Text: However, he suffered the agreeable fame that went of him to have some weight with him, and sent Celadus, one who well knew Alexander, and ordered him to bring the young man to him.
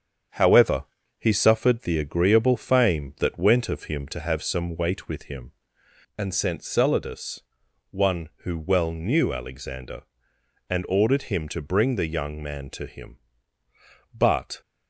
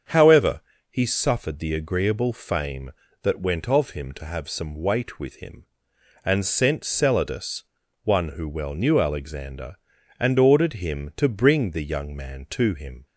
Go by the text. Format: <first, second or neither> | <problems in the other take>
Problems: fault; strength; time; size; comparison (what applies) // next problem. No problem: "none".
second | starts louder than the rest; strong; until 1.6 s; 7.5 dB; strong in the second // goes on to say "But"; slight; from 14.1 s on; 0.46 s long